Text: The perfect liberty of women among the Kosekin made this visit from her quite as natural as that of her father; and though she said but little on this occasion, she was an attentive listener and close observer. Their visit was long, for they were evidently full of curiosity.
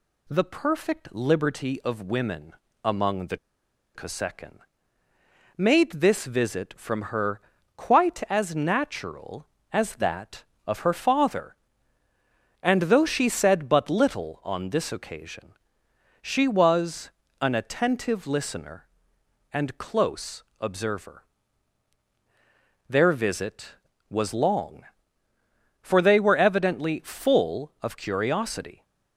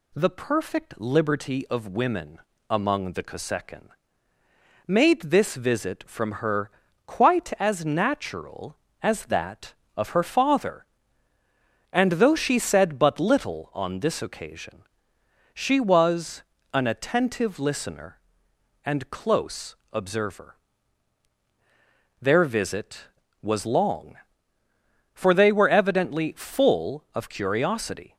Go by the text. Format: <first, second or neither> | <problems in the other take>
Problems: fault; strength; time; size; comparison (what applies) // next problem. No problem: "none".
second | pauses between "women" and "among"; slight; at 2.5 s; 0.32 s long; slight in the second // pauses between "the" and "Kosekin"; noticeable; at 3.3 s; 0.56 s long // pauses between "Kosekin" and "made"; noticeable; at 4.5 s; 0.98 s long; noticeable in the second // pauses between "her" and "quite"; at 7.3 s; 0.38 s long; also in the second // pauses between "was" and "an"; slight; at 17.1 s; 0.28 s long; slight in the second // pauses between "close" and "observer"; slight; at 20.4 s; 0.16 s long; slight in the second